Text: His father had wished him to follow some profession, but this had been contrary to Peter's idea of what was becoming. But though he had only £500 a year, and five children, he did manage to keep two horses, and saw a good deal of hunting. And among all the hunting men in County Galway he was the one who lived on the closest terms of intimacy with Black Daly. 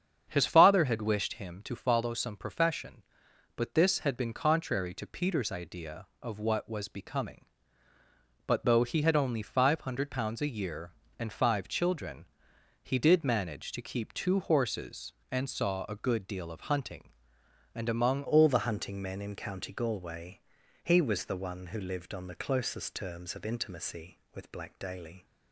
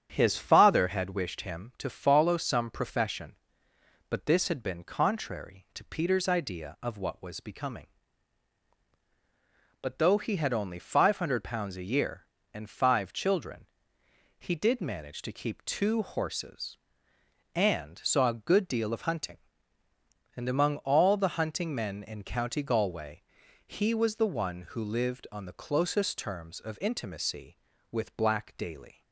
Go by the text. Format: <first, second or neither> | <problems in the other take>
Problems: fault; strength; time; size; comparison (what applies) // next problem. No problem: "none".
second | starts louder than the rest; strong; until 1.2 s; 8 dB; strong in the second // changes voice at "all"; from 18.2 s on; 7.0 s long // pauses between "Galway" and "he"; noticeable; at 20.3 s; 0.46 s long; also in the second